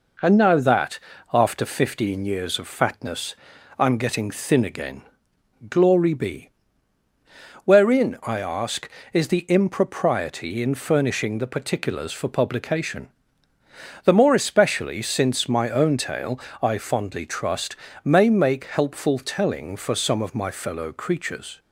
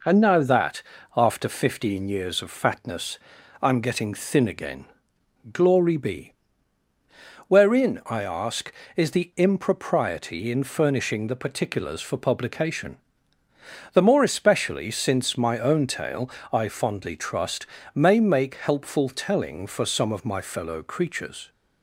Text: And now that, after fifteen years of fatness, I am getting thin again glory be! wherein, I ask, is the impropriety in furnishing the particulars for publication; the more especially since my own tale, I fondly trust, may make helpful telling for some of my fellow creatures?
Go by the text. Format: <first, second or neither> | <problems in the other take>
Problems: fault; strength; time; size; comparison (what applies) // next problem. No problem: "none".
neither | pauses between "again" and "glory"; noticeable; the same in both